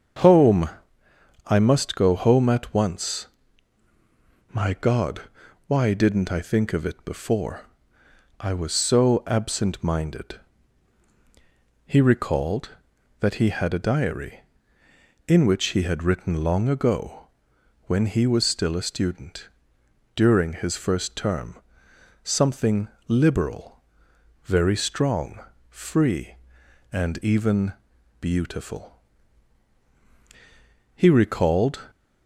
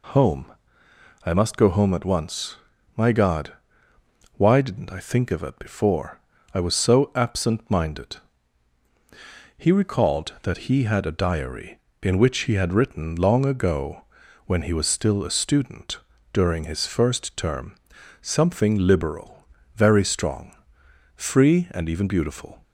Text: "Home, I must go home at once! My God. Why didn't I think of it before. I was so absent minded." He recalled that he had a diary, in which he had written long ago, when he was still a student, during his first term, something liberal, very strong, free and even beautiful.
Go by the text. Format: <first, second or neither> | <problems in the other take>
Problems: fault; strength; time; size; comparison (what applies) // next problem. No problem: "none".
second | starts louder than the rest; until 1.9 s; 7 dB // pauses between "something" and "liberal"; slight; at 22.8 s; 0.20 s long // pauses between "even" and "beautiful"; noticeable; at 27.7 s; 0.48 s long // goes on to say "He recalled"; noticeable; from 30.9 s on; 0.92 s long